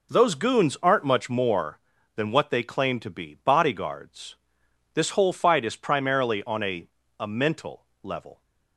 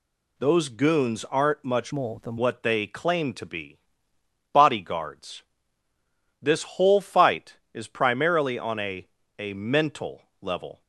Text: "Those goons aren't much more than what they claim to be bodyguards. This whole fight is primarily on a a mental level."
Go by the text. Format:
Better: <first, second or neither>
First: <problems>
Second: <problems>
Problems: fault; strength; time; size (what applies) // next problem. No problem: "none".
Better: first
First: pauses between "a" and "a"; slight; at 6.8 s; 0.32 s long // pauses between "mental" and "level"; slight; at 7.8 s; 0.18 s long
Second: changes voice from "more" to "than"; from 1.9 to 2.3 s; 0.4 s long // pauses between "be" and "bodyguards"; noticeable; at 3.7 s; 0.74 s long // pauses between "a" and "a"; slight; at 9.0 s; 0.32 s long // pauses between "mental" and "level"; slight; at 10.2 s; 0.18 s long